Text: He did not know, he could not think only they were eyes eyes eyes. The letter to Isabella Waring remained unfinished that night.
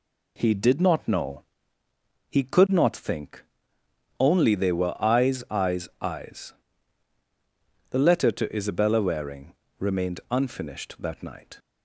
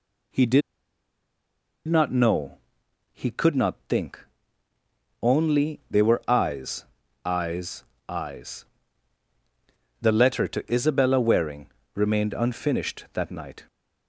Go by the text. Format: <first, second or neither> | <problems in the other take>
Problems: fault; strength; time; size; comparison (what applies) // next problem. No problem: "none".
first | pauses between "did" and "not"; strong; at 0.6 s; 1.2 s long // pauses between "think" and "only"; at 4.2 s; 1.0 s long; noticeable in the first // pauses between "eyes" and "eyes"; at 6.8 s; 0.40 s long // pauses between "eyes" and "eyes"; slight; at 7.8 s; 0.24 s long // pauses between "Waring" and "remained"; slight; at 11.7 s; 0.24 s long; slight in the first